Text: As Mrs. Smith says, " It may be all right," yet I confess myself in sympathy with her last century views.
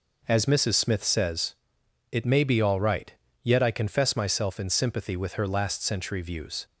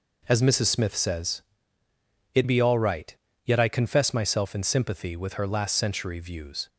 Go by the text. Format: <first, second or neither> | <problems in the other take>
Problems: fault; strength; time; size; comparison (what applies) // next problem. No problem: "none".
first | skips "may"; at 2.4 s